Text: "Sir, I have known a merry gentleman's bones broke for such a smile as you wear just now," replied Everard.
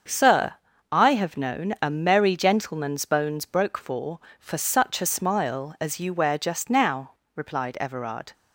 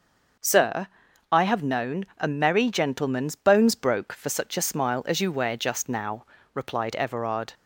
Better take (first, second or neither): second